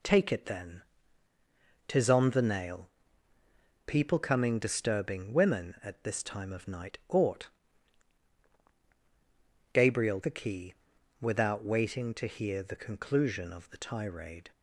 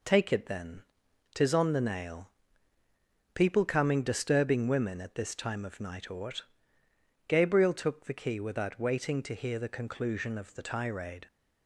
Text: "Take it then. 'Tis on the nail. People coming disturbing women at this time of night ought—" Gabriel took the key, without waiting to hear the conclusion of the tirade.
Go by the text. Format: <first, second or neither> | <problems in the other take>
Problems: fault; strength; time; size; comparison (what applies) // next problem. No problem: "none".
second | skips "took"; at 10.2 s